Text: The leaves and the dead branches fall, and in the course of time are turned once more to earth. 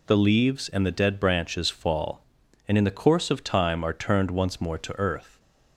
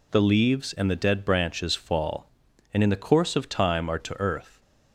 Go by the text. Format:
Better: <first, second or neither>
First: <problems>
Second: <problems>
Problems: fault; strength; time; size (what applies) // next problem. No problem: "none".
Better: first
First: none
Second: skips "turned once more"; at 3.9 s